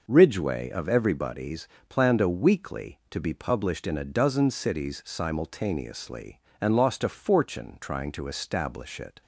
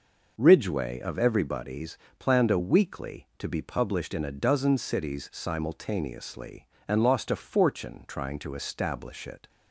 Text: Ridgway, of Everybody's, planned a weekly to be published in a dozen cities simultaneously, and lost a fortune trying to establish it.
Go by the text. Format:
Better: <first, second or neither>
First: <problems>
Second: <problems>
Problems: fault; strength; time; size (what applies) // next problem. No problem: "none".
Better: neither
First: none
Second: none